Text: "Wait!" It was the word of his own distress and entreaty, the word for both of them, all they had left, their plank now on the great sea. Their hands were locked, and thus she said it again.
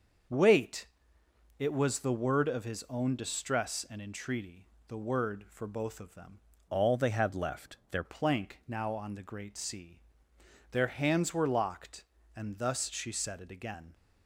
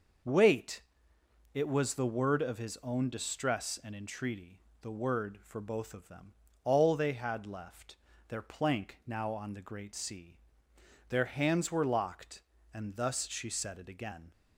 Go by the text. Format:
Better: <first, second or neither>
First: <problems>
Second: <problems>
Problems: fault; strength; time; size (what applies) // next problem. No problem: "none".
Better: second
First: starts louder than the rest; until 2.0 s; 6.5 dB // changes voice from "all" to "their"; from 6.6 to 8.0 s; 1.4 s long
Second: none